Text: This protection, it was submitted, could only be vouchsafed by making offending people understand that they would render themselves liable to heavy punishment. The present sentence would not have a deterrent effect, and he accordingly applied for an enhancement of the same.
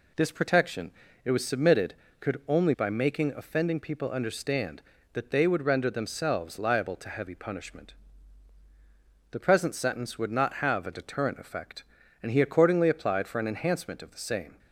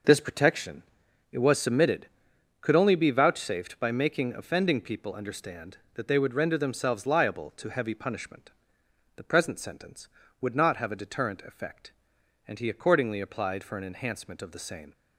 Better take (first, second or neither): second